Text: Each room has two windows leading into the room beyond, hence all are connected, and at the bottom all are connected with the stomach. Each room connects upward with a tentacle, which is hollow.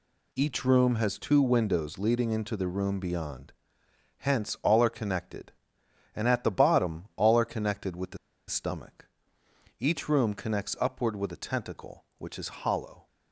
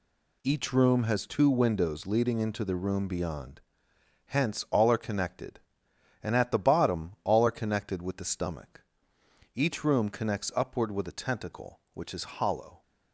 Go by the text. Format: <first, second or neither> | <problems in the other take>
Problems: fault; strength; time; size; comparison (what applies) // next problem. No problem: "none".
second | pauses between "the" and "stomach"; slight; at 8.1 s; 0.31 s long